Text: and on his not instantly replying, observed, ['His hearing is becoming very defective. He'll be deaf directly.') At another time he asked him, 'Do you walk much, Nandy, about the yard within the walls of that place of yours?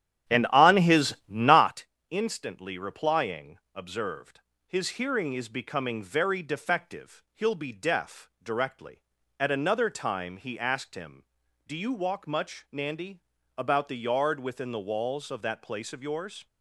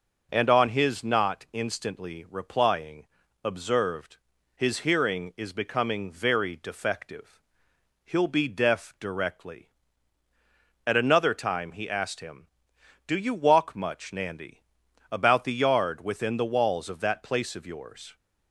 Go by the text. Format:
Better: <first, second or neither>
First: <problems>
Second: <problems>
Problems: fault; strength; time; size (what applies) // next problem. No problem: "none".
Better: second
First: starts louder than the rest; strong; until 1.9 s; 10 dB // pauses between "not" and "instantly"; slight; at 1.8 s; 0.26 s long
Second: none